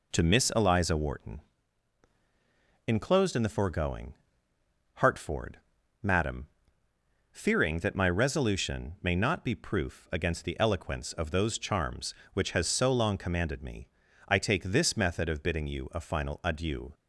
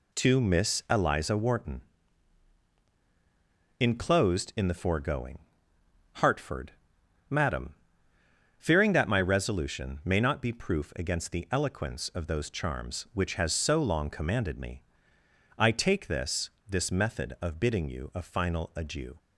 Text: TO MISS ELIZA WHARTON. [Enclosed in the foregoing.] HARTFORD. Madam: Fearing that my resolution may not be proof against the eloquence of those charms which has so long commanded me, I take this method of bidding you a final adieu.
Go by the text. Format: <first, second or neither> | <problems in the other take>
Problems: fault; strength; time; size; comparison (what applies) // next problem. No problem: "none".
first | says "this" twice; at 16.6 s